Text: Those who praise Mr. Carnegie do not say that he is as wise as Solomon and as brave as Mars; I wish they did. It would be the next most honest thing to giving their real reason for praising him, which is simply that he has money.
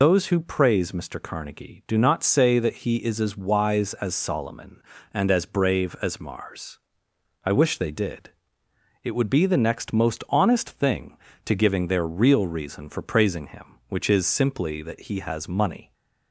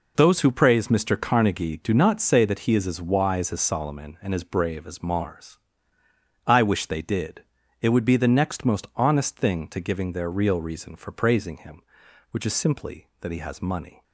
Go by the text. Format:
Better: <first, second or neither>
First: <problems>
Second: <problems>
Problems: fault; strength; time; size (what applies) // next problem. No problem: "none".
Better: second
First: loses the start of "Those"; at 0.0 s; 90 ms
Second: none